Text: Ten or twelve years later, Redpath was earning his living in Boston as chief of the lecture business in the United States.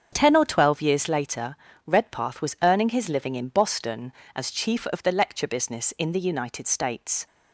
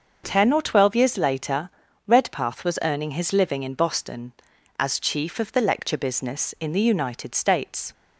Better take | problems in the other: neither | starts louder than the rest; the same in both

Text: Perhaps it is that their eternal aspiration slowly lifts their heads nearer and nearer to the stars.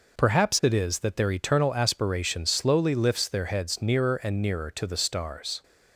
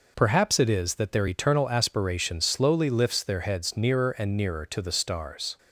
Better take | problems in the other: neither | none

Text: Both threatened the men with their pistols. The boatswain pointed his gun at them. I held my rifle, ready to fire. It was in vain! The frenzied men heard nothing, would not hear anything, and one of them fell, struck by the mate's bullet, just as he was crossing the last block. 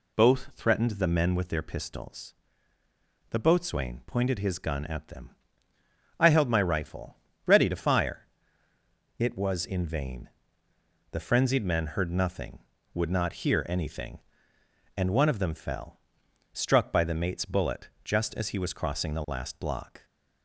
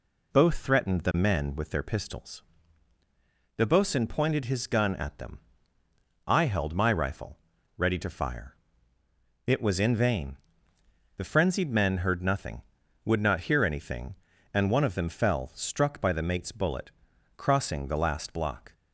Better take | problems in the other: first | skips "just as he was"; at 17.1 s

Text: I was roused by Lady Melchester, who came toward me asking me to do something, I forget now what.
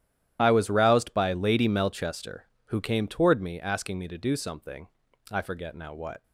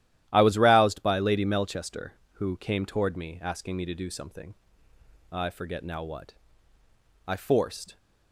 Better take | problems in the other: first | starts louder than the rest; strong; until 1.3 s; 13 dB; strong in the first // goes on to say "I forced"; noticeable; from 7.2 s on; 0.72 s long

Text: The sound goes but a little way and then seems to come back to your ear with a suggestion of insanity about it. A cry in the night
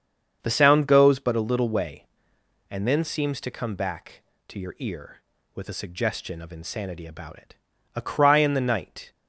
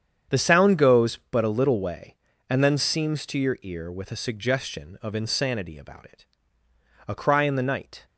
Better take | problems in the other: first | starts louder than the rest; strong; until 1.4 s; 8 dB; strong in the first // skips "to come back"; at 3.2 s

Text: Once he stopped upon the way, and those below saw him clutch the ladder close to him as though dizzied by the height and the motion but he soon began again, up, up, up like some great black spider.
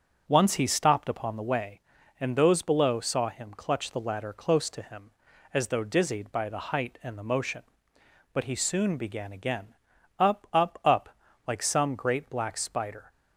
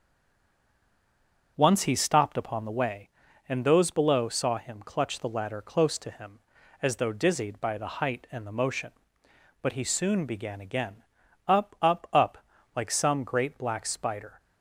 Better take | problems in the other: first | stays silent before the first word; noticeable; until 1.5 s; 1.5 s long // starts louder than the rest; noticeable; until 2.5 s; 6 dB; noticeable in the first // pauses between "up" and "like"; at 12.3 s; 0.40 s long; also in the first

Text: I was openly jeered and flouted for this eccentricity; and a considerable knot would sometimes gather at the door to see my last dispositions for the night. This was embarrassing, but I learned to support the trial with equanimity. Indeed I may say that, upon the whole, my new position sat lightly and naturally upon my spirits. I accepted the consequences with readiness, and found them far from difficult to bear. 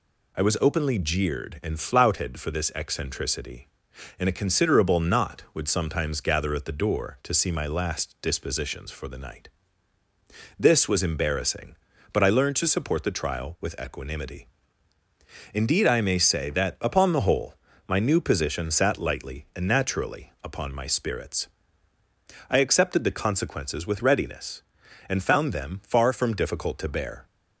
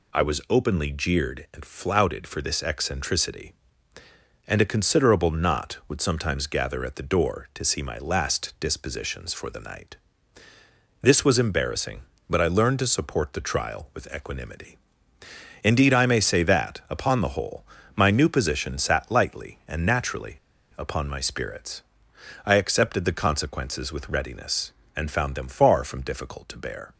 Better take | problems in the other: first | pauses between "naturally" and "upon"; at 20.3 s; 0.38 s long

